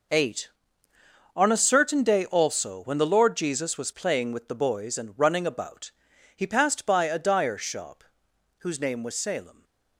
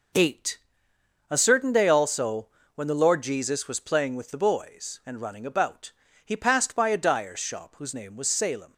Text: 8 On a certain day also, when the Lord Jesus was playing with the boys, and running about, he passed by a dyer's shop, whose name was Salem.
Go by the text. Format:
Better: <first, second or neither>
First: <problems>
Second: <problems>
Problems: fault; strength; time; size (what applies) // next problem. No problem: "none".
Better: first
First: none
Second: skips "On"; at 0.9 s